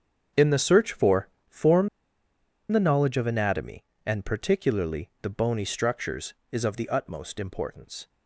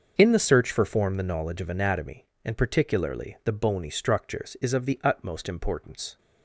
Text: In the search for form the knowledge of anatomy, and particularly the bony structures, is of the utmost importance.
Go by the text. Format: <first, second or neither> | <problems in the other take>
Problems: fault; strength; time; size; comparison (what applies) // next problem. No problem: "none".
second | starts louder than the rest; strong; until 1.5 s; 7.5 dB; also in the second // pauses between "for" and "form"; slight; at 1.2 s; 0.20 s long // pauses between "form" and "the"; noticeable; at 1.8 s; 0.83 s long